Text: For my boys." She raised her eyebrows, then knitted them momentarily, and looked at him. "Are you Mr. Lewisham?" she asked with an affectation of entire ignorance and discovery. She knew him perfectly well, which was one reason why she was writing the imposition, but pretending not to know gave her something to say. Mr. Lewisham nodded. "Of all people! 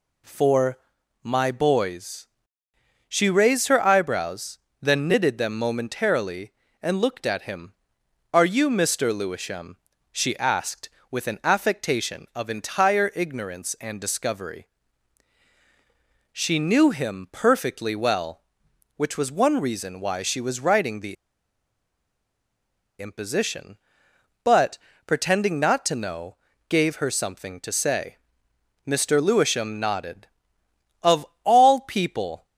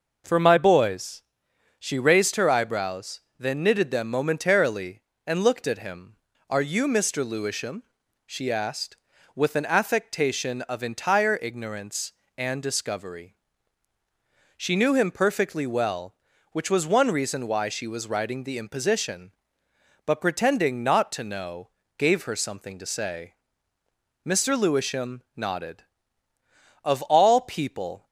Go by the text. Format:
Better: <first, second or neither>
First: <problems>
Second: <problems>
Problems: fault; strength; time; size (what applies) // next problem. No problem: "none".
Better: second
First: pauses between "For" and "my"; at 0.7 s; 0.44 s long // pauses between "the" and "imposition"; strong; at 21.1 s; 1.8 s long // pauses between "but" and "pretending"; slight; at 24.7 s; 0.26 s long // pauses between "know" and "gave"; slight; at 26.3 s; 0.32 s long // pauses between "Of" and "all"; slight; at 31.2 s; 0.20 s long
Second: pauses between "know" and "gave"; slight; at 21.7 s; 0.28 s long